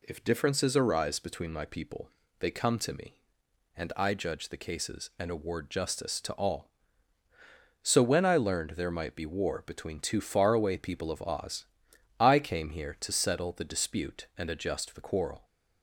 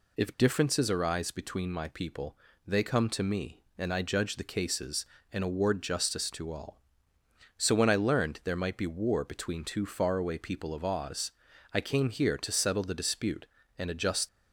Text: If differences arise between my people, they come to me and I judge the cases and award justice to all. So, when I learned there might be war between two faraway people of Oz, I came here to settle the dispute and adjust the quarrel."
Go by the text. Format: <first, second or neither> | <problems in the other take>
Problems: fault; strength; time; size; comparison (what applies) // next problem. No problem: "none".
first | stops before "the quarrel"; at 14.2 s